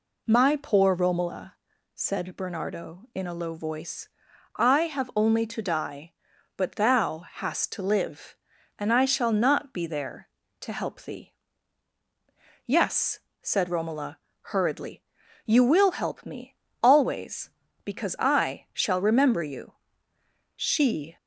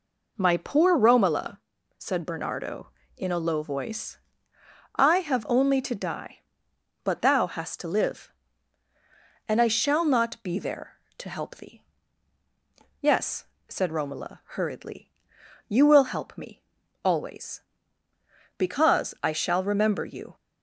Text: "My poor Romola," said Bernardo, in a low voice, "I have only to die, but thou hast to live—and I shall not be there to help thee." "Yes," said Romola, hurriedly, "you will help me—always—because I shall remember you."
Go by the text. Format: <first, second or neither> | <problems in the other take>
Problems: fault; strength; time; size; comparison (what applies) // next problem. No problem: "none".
second | goes on to say "She"; noticeable; from 20.5 s on; 0.62 s long